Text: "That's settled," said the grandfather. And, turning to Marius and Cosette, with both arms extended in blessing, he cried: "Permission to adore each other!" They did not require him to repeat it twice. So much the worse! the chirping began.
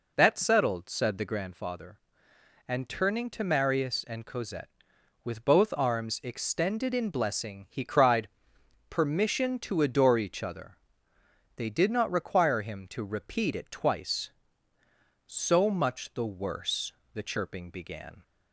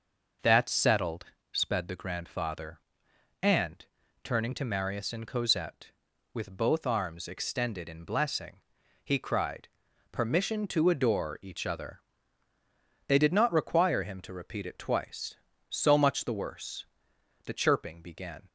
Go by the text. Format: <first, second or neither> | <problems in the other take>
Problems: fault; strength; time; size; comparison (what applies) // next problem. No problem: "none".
first | says "sped" for "said"; at 1.5 s